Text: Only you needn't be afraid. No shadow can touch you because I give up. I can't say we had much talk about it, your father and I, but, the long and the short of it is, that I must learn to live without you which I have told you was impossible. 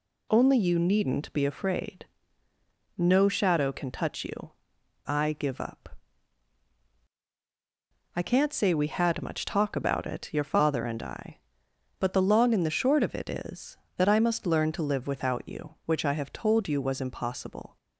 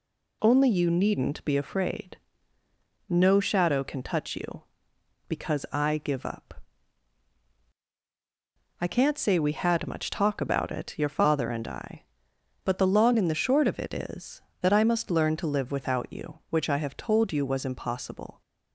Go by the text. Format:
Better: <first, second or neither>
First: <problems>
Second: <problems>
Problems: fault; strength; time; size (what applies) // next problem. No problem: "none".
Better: second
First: skips "because"; at 4.7 s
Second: none